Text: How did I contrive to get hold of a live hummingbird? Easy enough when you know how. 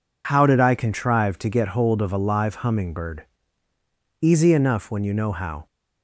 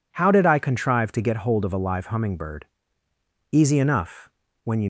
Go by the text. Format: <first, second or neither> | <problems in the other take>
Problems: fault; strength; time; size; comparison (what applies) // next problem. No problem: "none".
first | pauses between "enough" and "when"; slight; at 4.2 s; 0.36 s long // stops before "know how"; at 4.8 s